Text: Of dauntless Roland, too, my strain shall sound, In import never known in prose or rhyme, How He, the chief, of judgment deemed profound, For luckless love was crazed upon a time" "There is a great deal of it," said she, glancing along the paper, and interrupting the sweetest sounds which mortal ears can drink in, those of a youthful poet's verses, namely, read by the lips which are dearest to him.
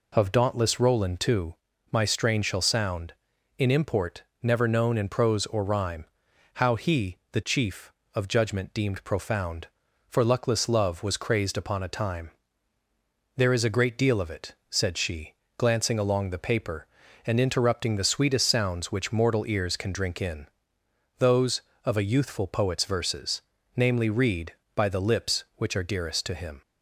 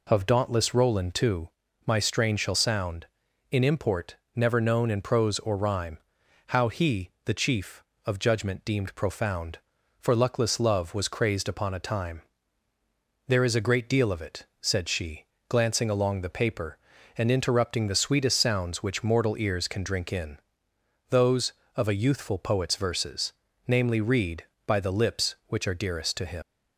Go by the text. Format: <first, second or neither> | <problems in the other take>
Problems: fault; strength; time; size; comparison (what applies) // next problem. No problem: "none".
first | pauses between "import" and "never"; slight; at 4.1 s; 0.22 s long; slight in the first // pauses between "time" and "There"; at 12.2 s; 1.0 s long; also in the first // leaves "him" unfinished; at 26.4 s; 100 ms